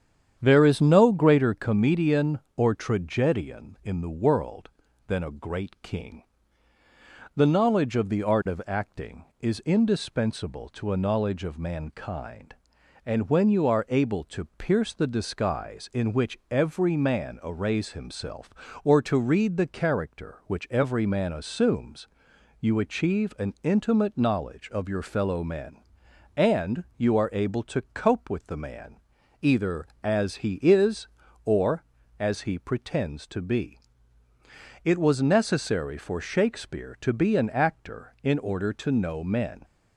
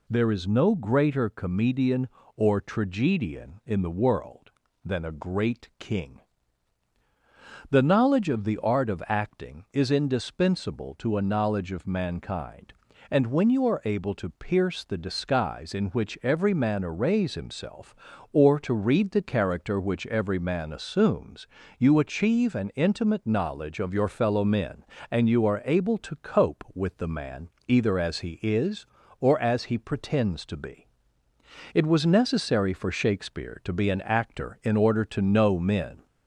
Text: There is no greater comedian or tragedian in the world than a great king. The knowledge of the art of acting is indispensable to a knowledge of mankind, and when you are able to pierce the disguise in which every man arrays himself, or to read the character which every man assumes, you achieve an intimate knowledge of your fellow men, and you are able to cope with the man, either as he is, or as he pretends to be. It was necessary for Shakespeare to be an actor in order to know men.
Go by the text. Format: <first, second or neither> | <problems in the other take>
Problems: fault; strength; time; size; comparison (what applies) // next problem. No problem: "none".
second | starts louder than the rest; strong; until 1.6 s; 8.5 dB